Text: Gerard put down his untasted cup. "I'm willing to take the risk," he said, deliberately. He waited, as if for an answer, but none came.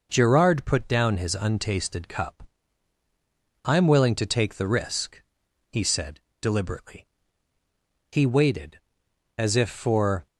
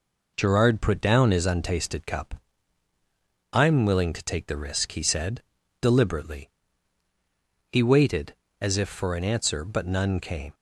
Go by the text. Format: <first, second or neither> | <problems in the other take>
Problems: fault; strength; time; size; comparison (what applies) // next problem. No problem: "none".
second | stops before "an answer but none came"; at 10.2 s